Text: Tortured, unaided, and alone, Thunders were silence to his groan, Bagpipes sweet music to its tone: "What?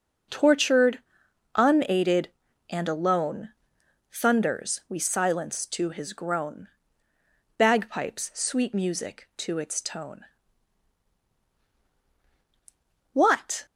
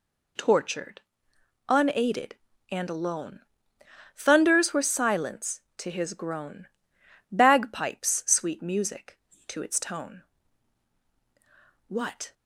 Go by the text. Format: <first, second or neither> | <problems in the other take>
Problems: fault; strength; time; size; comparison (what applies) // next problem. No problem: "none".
second | says "we" for "were"; at 4.8 s